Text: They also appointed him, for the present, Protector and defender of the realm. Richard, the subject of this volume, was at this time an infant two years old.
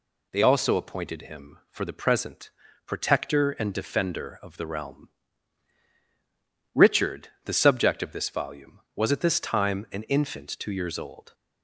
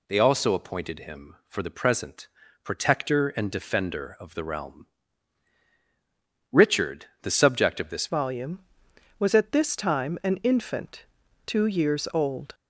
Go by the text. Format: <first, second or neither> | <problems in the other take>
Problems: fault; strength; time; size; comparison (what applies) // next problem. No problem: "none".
first | changes voice at "volume"; from 8.0 s on; 4.5 s long // pauses between "infant" and "two"; at 11.0 s; 0.42 s long